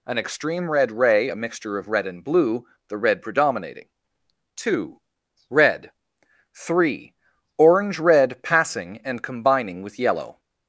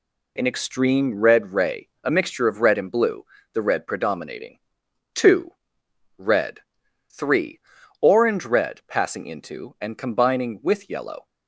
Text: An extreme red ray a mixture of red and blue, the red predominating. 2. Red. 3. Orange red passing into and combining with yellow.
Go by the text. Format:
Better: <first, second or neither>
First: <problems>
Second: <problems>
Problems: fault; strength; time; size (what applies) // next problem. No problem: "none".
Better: second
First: skips "into"; at 9.0 s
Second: none